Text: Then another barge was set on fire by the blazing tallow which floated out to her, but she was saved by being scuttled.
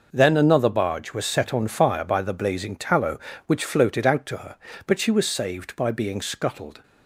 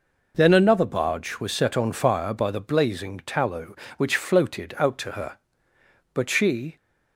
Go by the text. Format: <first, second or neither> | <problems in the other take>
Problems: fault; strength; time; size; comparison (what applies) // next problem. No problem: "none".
first | stops before "was saved by being scuttled"; at 6.7 s